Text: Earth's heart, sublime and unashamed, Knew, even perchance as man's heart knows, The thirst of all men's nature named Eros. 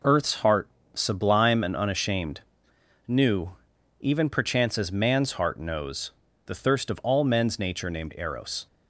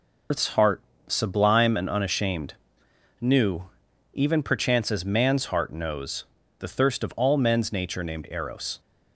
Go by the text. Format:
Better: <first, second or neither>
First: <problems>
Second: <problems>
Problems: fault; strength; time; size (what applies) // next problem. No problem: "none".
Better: first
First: none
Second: loses the start of "Earth's"; at 0.3 s; 155 ms